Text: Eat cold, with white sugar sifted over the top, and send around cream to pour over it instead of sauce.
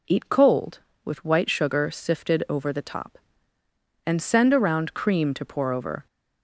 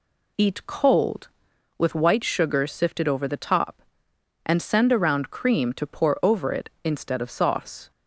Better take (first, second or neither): second